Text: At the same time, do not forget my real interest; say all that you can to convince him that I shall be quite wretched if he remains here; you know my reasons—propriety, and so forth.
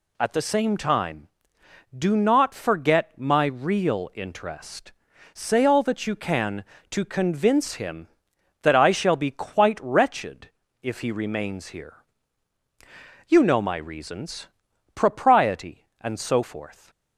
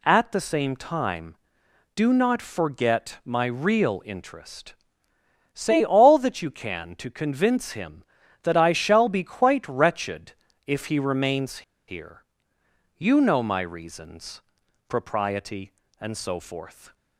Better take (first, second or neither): first